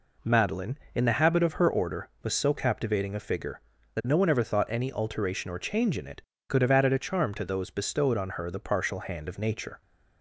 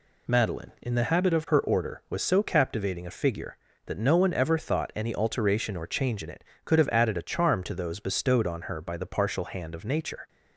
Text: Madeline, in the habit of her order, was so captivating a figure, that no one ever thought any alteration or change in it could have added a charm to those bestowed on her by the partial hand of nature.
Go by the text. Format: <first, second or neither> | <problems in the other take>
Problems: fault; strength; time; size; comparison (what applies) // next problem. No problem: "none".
second | skips "by"; at 8.4 s